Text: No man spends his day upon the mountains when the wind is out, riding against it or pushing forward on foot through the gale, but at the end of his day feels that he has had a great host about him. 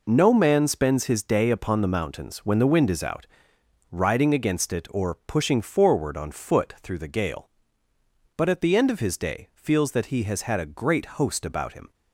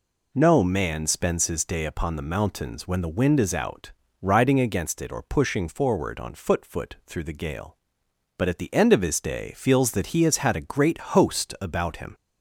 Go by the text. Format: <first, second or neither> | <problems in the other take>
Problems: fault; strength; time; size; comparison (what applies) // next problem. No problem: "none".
first | says "foot" twice; at 6.6 s